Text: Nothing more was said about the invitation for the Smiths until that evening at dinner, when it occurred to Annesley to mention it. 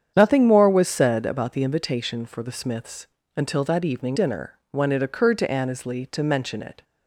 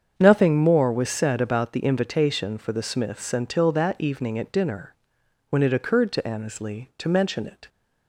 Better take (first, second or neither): second